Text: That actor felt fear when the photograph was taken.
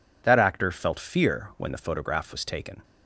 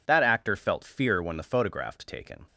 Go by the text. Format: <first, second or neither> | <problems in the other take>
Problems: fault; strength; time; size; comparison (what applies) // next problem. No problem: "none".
first | skips "was"; at 1.9 s